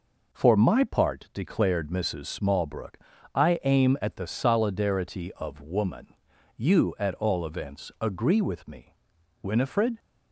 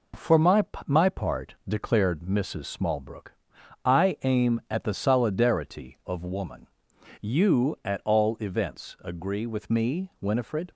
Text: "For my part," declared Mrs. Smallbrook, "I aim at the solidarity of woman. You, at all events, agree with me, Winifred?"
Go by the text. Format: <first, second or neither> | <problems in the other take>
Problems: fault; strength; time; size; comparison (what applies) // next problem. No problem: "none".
first | says "my" twice; at 0.8 s